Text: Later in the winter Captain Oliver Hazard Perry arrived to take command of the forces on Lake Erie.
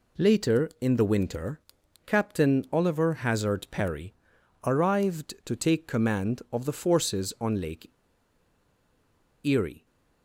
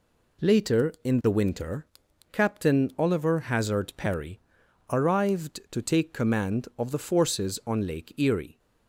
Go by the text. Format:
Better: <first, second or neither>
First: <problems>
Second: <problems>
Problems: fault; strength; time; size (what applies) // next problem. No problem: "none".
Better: second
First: pauses between "winter" and "Captain"; noticeable; at 1.6 s; 0.46 s long // pauses between "Perry" and "arrived"; noticeable; at 4.1 s; 0.50 s long // pauses between "Lake" and "Erie"; strong; at 7.8 s; 1.5 s long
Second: pauses between "winter" and "Captain"; noticeable; at 1.8 s; 0.46 s long // pauses between "Perry" and "arrived"; noticeable; at 4.4 s; 0.50 s long